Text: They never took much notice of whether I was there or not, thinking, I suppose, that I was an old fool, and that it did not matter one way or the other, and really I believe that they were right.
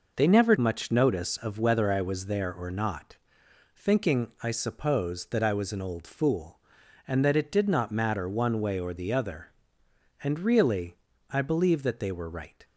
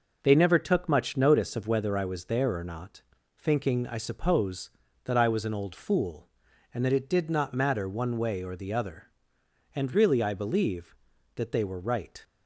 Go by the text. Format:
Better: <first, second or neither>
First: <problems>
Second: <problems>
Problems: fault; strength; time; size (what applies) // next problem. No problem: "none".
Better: second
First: skips "took"; at 0.5 s // pauses between "really" and "I"; slight; at 10.9 s; 0.34 s long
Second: none